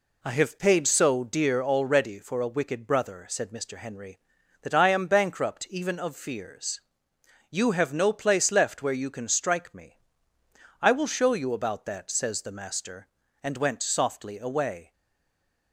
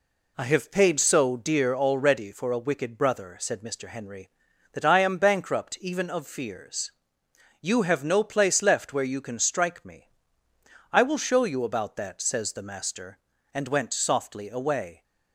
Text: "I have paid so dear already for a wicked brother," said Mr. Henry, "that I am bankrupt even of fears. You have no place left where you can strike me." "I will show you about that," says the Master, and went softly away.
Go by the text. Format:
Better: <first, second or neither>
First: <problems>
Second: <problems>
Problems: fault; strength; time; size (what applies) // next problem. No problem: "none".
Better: second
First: stays silent after the last word; slight; from 14.9 s on; 0.8 s long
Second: none